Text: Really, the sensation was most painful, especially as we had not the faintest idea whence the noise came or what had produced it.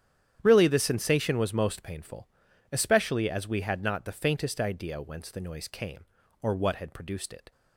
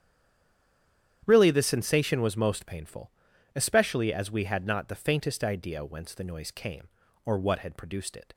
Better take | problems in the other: first | stays silent before the first word; noticeable; until 1.2 s; 1.2 s long // starts louder than the rest; strong; until 2.2 s; 10 dB; strong in the first

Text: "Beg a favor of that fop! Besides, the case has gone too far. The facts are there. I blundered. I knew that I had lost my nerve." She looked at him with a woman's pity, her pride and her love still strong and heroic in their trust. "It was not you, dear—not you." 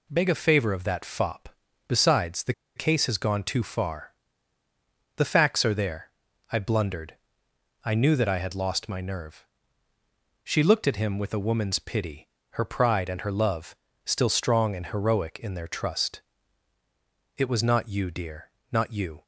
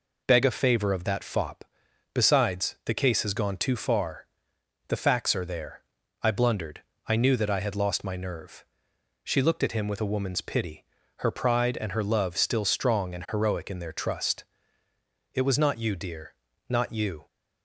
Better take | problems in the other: second | pauses between "the" and "case"; slight; at 2.5 s; 0.22 s long // pauses between "love" and "still"; slight; at 13.7 s; 0.30 s long

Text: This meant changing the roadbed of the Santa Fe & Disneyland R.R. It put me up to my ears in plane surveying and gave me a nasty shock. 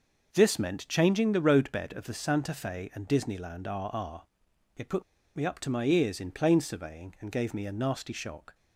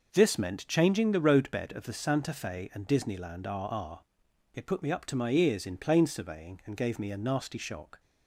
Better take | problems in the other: second | pauses between "put" and "me"; slight; at 5.0 s; 0.32 s long

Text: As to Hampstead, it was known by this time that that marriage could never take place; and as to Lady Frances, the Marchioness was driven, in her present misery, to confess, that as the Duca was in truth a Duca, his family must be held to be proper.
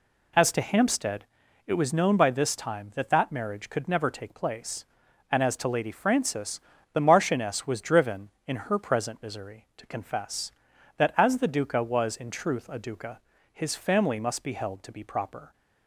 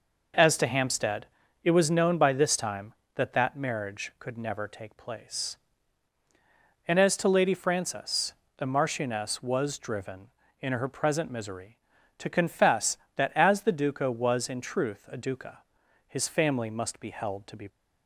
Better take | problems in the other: first | stops before "proper"; at 17.6 s

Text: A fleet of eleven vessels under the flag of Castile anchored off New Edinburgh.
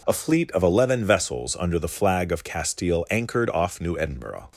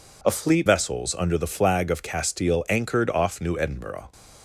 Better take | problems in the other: first | skips "of eleven"; at 0.6 s

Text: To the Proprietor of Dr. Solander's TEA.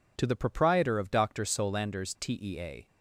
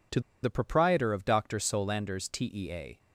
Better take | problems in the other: first | pauses between "To" and "the"; slight; at 0.1 s; 0.23 s long

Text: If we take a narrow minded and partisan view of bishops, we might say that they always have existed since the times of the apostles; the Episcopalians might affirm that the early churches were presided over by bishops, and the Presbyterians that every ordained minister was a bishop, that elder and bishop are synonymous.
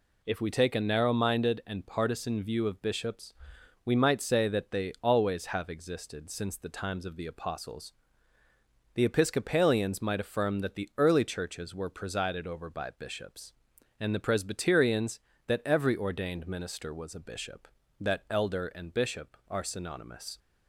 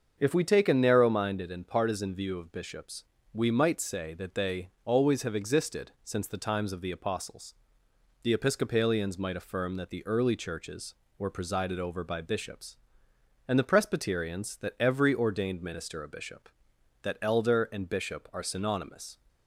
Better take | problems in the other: first | starts louder than the rest; until 1.1 s; 7 dB // skips "was"; at 16.0 s

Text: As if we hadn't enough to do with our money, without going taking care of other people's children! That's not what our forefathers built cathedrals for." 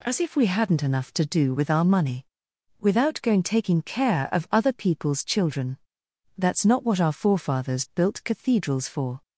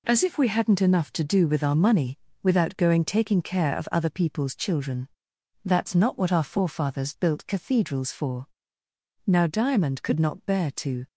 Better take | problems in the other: first | goes on to say "Now Diamond could not bear to"; strong; from 9.2 s on; 1.8 s long

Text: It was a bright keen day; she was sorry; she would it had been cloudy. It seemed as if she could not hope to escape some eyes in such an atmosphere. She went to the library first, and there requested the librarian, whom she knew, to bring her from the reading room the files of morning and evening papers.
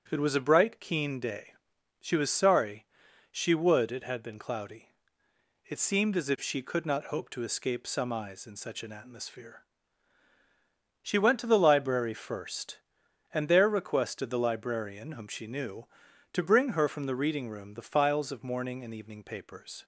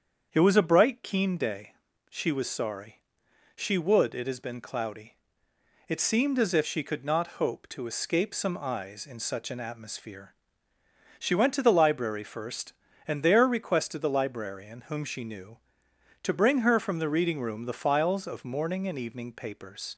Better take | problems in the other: first | starts louder than the rest; strong; until 1.3 s; 7.5 dB; strong in the first // says "has" for "had"; at 4.2 s

